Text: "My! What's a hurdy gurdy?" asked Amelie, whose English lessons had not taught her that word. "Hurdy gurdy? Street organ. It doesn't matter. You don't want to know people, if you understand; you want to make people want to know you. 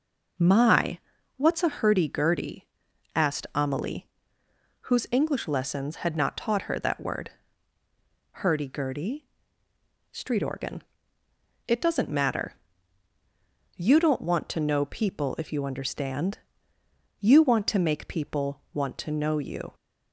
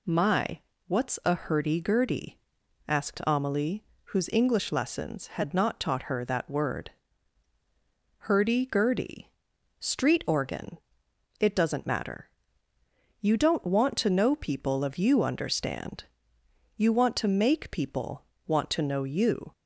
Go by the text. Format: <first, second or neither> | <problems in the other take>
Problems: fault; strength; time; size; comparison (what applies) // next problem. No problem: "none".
first | says "of" for "if"; at 14.8 s // pauses between "people" and "want"; slight; at 18.2 s; 0.22 s long